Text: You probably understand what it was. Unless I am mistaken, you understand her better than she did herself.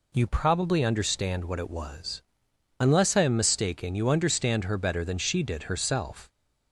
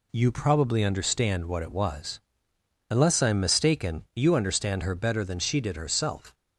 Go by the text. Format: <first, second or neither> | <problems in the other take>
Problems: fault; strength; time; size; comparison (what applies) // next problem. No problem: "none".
neither | none